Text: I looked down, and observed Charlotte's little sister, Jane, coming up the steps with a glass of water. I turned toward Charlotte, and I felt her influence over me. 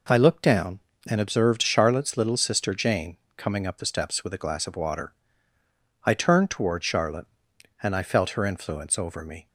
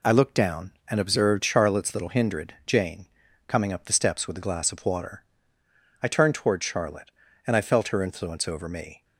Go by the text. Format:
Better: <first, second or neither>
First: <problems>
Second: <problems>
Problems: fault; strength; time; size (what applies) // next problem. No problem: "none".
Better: first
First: none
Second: says "hindred" for "sister"; at 2.0 s